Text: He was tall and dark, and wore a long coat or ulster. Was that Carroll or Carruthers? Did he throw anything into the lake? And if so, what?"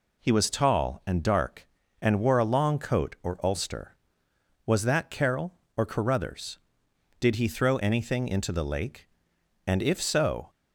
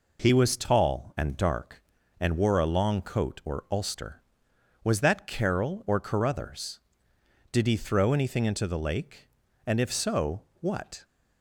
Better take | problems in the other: second | stops before "what"; at 10.5 s

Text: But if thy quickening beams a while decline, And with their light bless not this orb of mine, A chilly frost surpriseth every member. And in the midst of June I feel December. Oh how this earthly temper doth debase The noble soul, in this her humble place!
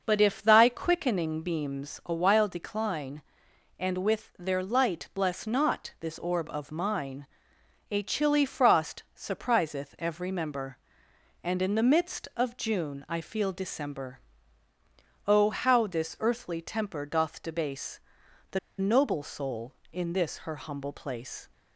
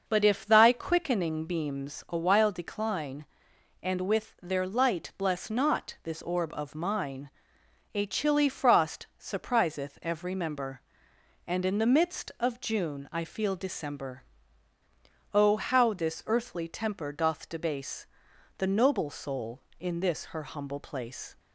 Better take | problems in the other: second | starts louder than the rest; noticeable; until 1.0 s; 6 dB; noticeable in the second // pauses between "debase" and "The"; noticeable; at 18.0 s; 0.50 s long; noticeable in the second // pauses between "The" and "noble"; slight; at 18.5 s; 0.20 s long

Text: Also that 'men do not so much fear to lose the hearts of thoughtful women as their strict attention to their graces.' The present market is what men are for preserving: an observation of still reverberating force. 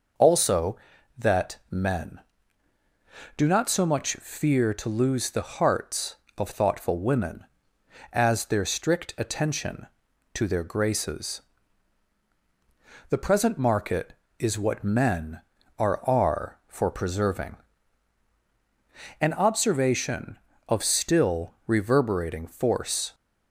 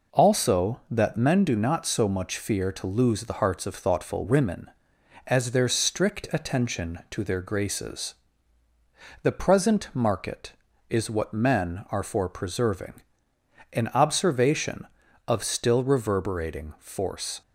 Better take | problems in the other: second | says "are" twice; at 16.0 s

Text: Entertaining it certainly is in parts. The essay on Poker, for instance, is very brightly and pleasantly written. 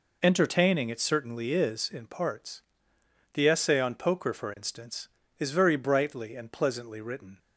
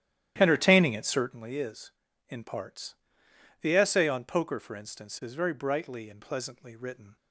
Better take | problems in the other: first | starts louder than the rest; strong; until 1.4 s; 12.5 dB

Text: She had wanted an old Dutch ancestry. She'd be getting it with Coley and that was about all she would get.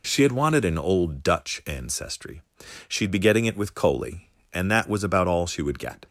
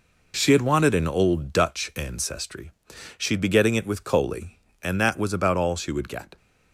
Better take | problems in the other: first | gets quieter; throughout; 6.5 dB

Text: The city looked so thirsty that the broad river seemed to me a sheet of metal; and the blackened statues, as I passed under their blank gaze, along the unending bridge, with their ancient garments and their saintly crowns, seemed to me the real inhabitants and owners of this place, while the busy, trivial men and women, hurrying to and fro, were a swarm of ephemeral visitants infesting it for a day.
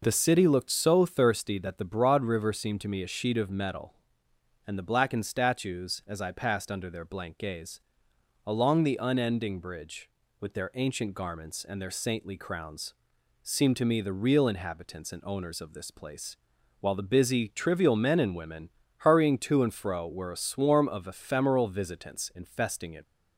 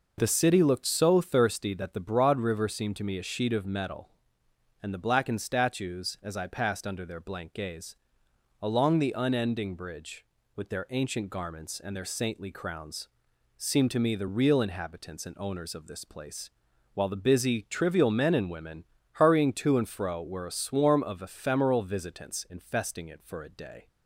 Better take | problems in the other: second | stops before "for a day"; at 23.0 s

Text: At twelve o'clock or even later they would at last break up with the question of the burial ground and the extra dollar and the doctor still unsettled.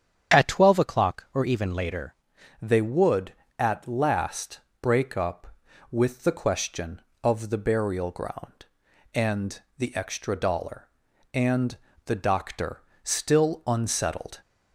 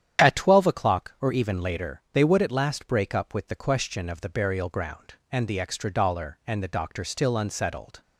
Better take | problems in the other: second | starts louder than the rest; strong; until 1.4 s; 8 dB; strong in the second // changes voice at "they"; from 2.6 s on; 11.8 s long // pauses between "last" and "break"; slight; at 4.5 s; 0.24 s long // pauses between "and" and "the"; slight; at 9.6 s; 0.18 s long // pauses between "and" and "the"; slight; at 11.7 s; 0.28 s long // pauses between "doctor" and "still"; slight; at 12.8 s; 0.20 s long

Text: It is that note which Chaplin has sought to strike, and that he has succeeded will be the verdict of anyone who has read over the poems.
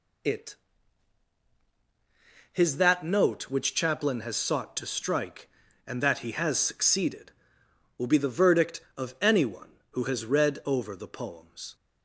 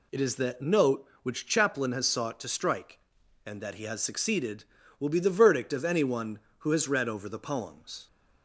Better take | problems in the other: second | says "his" for "is"; at 2.5 s

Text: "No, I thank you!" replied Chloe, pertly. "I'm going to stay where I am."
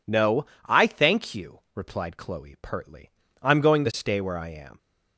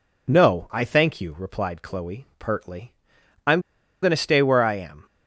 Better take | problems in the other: first | pauses between "I'm" and "going"; at 3.6 s; 0.41 s long

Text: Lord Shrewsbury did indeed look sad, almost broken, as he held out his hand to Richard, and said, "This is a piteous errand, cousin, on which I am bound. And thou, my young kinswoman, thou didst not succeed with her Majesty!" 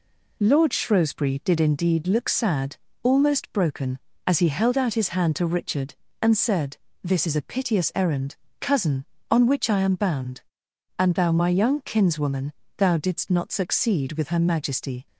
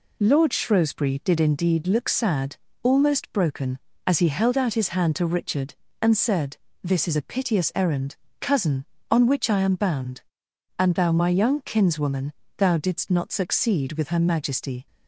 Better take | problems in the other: neither | none

